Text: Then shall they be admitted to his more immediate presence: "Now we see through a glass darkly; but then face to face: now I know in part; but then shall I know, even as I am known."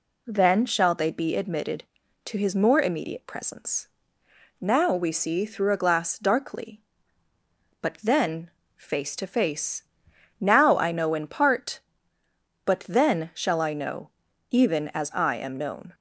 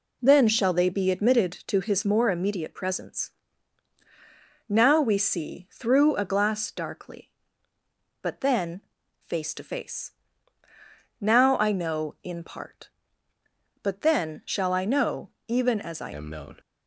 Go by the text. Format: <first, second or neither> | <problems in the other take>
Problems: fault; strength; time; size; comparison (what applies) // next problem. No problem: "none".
first | pauses between "then" and "face"; at 8.8 s; 0.40 s long; slight in the first // changes voice at "am"; from 16.1 s on; 0.4 s long